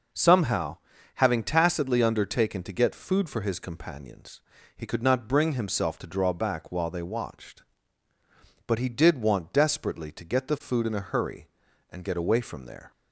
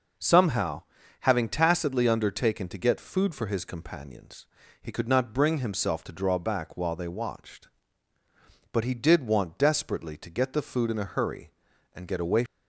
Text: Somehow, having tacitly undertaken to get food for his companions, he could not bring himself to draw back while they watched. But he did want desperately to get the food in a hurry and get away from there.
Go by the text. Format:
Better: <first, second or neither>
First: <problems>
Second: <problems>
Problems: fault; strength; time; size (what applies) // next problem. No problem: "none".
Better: first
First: none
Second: stops before "from there"; at 12.4 s